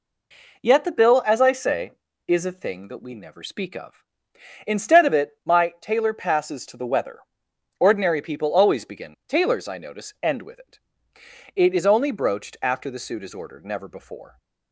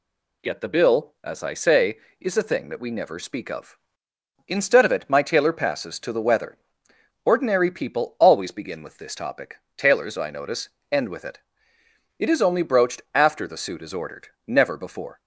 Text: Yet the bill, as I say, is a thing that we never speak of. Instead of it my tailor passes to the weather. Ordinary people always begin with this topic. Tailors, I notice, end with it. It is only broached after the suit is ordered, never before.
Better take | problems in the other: second | skips "with this topic"; at 9.2 s

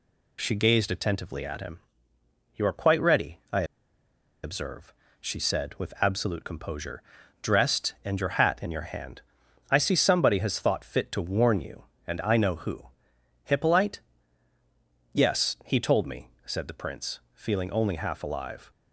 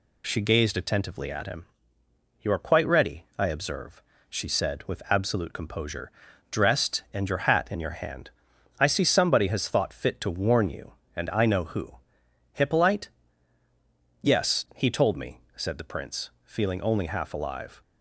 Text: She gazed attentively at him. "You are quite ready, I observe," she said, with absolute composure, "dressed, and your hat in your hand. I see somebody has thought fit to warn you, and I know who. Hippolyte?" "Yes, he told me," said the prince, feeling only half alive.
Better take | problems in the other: second | pauses between "I" and "observe"; noticeable; at 3.6 s; 0.80 s long

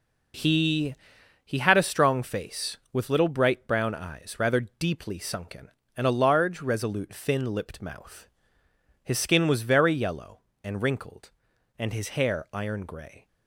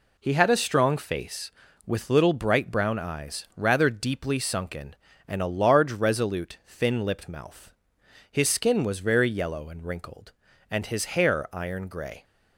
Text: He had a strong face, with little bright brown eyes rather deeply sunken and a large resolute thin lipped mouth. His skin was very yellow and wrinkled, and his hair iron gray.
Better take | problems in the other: second | says "He" twice; at 1.4 s

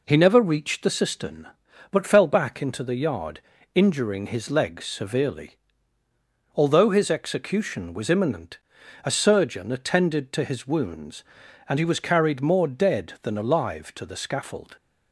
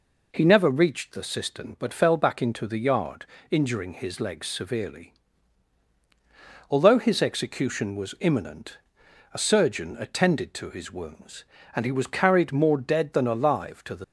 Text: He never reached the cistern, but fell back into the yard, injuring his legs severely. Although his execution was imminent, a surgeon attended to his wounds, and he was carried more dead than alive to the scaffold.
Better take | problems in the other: first | stops before "scaffold"; at 14.0 s

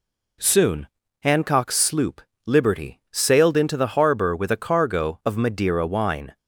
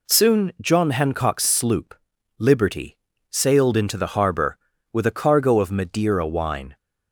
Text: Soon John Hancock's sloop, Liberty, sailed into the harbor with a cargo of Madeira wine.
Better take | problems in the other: second | skips "John"; at 1.0 s

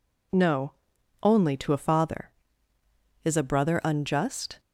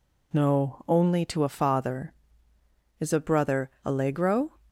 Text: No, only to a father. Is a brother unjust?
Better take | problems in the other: first | says "allegro" for "unjust"; at 3.8 s

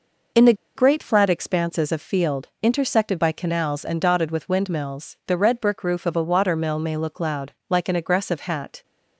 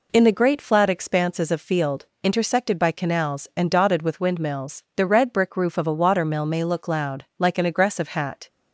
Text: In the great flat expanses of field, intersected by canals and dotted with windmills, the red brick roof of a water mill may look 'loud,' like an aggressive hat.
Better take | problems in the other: second | pauses between "the" and "great"; slight; at 0.5 s; 0.22 s long

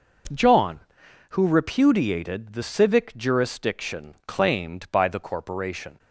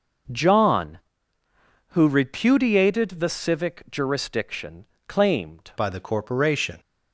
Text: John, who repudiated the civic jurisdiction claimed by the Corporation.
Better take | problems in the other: first | pauses between "jurisdiction" and "claimed"; slight; at 4.8 s; 0.20 s long // changes voice at "by"; from 5.7 s on; 1.0 s long

